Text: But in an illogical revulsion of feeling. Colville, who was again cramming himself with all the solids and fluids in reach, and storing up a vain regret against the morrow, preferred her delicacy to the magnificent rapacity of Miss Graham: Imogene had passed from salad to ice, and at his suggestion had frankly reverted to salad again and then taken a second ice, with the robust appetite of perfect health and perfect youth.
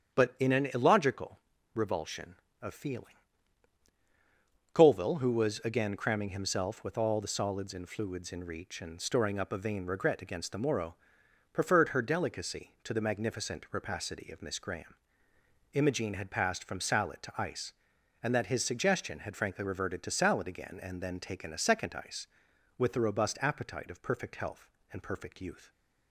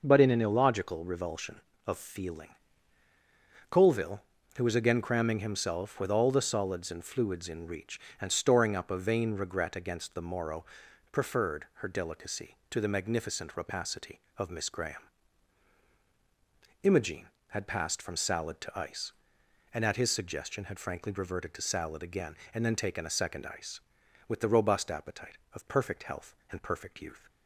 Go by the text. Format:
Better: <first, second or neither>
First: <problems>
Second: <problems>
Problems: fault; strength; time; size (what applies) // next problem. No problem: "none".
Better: second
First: starts louder than the rest; strong; until 1.2 s; 8.5 dB // pauses between "illogical" and "revulsion"; slight; at 1.3 s; 0.36 s long // says "that" for "at"; at 18.3 s // stays silent after the last word; slight; from 25.6 s on; 0.5 s long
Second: none